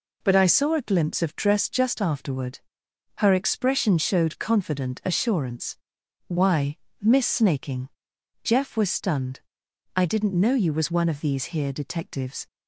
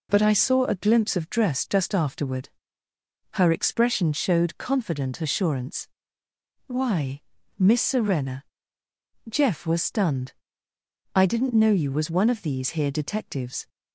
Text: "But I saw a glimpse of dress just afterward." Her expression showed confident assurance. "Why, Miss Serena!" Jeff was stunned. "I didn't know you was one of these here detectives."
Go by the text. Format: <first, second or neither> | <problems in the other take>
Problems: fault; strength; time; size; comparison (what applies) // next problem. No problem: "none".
second | says "Snaking" for "Serena"; at 7.2 s